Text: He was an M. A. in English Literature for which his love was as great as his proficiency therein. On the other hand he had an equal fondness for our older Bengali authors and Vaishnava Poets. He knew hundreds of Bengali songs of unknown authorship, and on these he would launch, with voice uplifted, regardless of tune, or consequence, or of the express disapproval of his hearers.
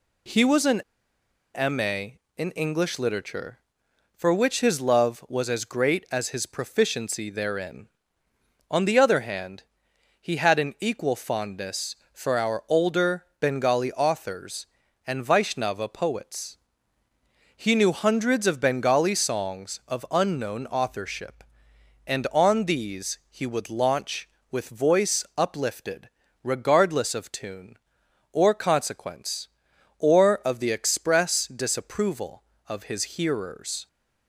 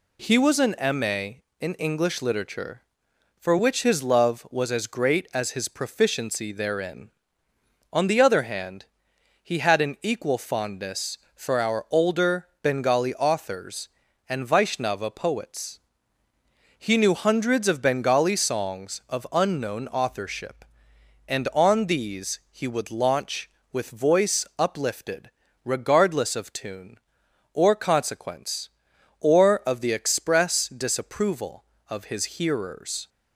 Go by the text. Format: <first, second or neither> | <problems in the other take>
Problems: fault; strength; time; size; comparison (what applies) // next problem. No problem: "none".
second | pauses between "an" and "M"; noticeable; at 0.8 s; 0.73 s long // pauses between "hand" and "he"; noticeable; at 9.6 s; 0.58 s long; noticeable in the second